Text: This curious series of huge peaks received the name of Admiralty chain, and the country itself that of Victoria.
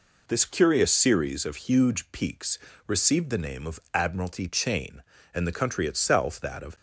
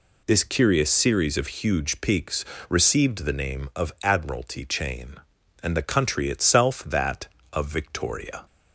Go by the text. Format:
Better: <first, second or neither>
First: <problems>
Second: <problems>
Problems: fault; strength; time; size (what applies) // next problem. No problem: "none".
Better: second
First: pauses between "peaks" and "received"; slight; at 2.5 s; 0.30 s long // pauses between "of" and "Admiralty"; slight; at 3.7 s; 0.16 s long // stops before "Victoria"; at 6.7 s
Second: pauses between "peaks" and "received"; slight; at 2.4 s; 0.24 s long